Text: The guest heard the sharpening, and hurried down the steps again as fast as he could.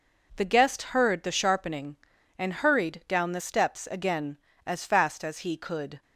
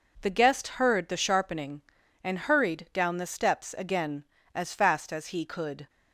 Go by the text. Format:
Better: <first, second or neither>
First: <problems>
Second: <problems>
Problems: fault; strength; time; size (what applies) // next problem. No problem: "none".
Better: neither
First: none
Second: none